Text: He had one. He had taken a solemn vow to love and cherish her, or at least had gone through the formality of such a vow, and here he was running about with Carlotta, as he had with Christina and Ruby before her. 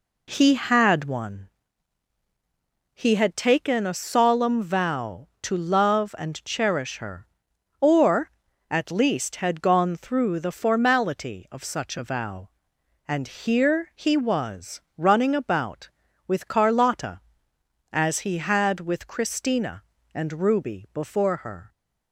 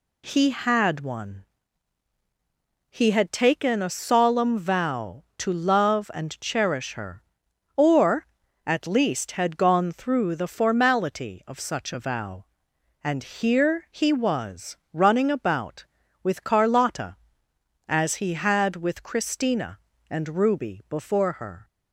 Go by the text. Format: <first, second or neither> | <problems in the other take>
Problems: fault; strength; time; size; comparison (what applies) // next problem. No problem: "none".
second | starts louder than the rest; slight; until 1.4 s; 2.5 dB // pauses between "was" and "running"; slight; at 14.8 s; 0.18 s long; slight in the second